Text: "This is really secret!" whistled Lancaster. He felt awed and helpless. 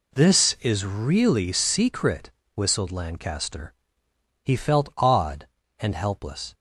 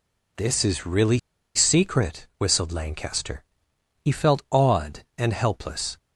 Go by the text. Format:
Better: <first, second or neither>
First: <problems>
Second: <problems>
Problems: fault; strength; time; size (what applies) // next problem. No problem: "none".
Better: first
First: none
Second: pauses between "really" and "secret"; at 1.1 s; 0.36 s long